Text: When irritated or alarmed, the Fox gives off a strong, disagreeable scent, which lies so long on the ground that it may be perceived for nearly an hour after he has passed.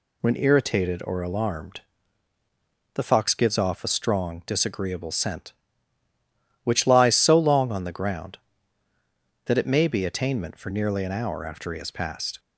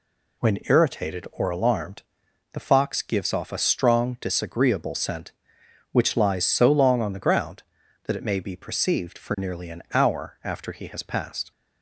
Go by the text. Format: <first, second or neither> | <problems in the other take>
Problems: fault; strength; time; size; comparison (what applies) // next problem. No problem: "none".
second | says "attainment" for "perceived"; at 10.0 s